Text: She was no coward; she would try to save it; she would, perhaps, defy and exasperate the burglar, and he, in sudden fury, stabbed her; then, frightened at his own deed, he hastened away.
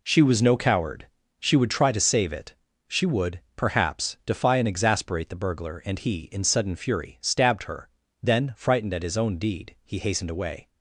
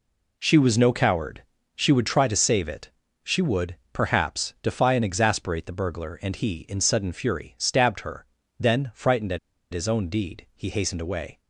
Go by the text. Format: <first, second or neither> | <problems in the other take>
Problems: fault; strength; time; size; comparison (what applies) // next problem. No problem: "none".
first | pauses between "at" and "his"; slight; at 9.3 s; 0.35 s long